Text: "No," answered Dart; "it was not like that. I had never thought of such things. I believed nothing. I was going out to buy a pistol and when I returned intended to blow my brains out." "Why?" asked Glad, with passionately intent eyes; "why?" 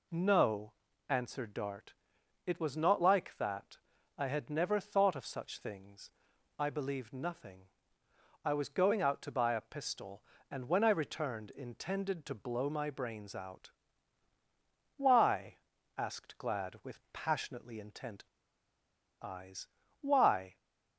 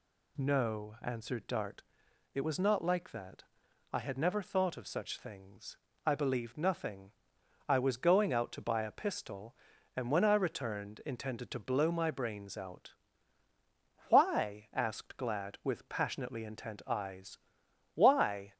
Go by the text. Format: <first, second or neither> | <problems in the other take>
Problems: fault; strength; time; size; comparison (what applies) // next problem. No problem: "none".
second | pauses between "intent" and "eyes"; at 18.2 s; 0.98 s long